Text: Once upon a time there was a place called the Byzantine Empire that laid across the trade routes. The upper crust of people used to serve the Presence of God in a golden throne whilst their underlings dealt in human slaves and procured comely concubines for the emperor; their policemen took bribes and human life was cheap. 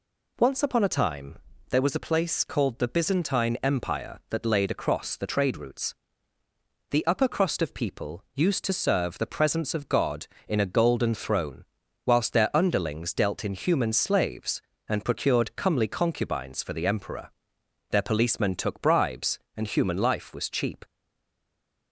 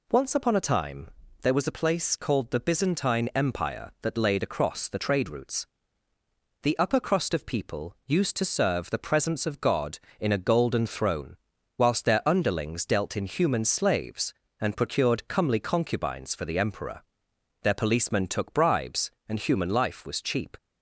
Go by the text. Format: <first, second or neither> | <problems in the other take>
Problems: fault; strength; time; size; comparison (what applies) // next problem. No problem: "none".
second | pauses between "time" and "there"; slight; at 1.3 s; 0.32 s long; slight in the second // pauses between "throne" and "whilst"; at 11.6 s; 0.42 s long; also in the second // stays silent after the last word; from 20.8 s on; 1.1 s long